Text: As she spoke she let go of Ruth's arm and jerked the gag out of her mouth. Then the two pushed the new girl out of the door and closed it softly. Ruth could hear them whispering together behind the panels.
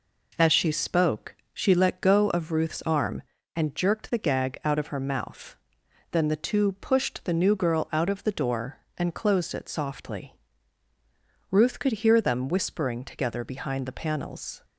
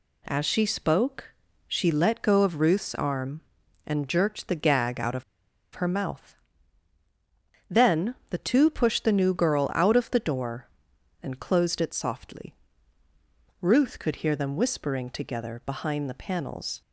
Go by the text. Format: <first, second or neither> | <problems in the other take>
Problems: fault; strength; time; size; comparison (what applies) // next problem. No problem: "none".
first | pauses between "spoke" and "she"; slight; at 1.3 s; 0.36 s long; slight in the first // pauses between "of" and "her"; noticeable; at 5.2 s; 0.51 s long